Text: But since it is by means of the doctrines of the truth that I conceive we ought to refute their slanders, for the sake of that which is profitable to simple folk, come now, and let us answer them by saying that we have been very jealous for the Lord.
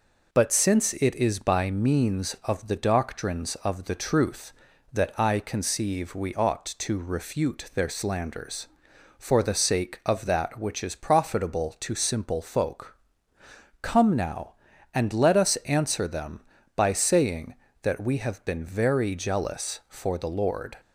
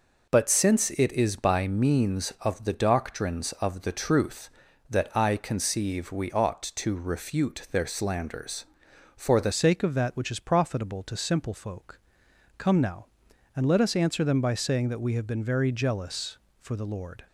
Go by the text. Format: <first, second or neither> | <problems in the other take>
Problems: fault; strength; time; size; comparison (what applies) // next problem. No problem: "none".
first | changes voice at "sake"; from 9.5 s on; 7.7 s long